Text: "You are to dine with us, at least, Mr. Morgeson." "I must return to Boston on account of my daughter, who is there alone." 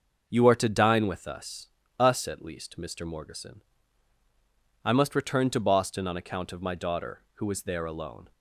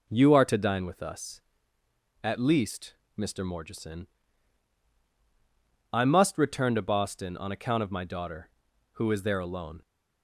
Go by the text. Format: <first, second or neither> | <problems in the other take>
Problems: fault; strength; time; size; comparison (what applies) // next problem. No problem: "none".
second | starts louder than the rest; noticeable; until 1.3 s; 6 dB // says "us" twice; at 1.9 s